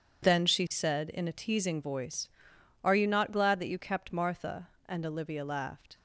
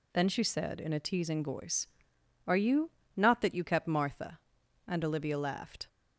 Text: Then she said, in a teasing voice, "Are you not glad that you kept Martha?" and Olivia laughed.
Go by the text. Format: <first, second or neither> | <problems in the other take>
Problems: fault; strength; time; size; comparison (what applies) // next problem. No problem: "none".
first | pauses between "you" and "not"; slight; at 2.9 s; 0.26 s long // skips "glad"; at 3.4 s